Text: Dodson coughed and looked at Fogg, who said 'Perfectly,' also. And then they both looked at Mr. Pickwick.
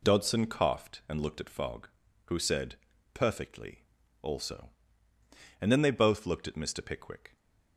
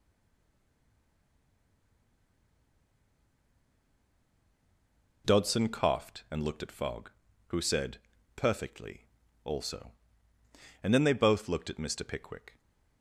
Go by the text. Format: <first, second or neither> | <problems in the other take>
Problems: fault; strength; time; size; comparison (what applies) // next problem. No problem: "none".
first | stays silent before the first word; strong; until 5.2 s; 5.2 s long // pauses between "said" and "Perfectly"; at 7.9 s; 0.38 s long; also in the first